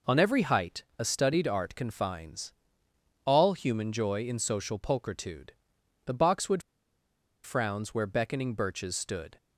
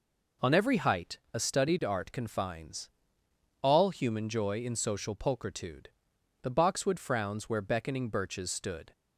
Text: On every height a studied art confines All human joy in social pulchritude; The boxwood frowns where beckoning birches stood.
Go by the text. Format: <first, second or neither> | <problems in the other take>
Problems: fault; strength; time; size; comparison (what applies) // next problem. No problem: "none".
second | pauses between "height" and "a"; slight; at 0.8 s; 0.16 s long; slight in the second // pauses between "confines" and "All"; noticeable; at 2.5 s; 0.72 s long; noticeable in the second // pauses between "boxwood" and "frowns"; noticeable; at 6.6 s; 0.82 s long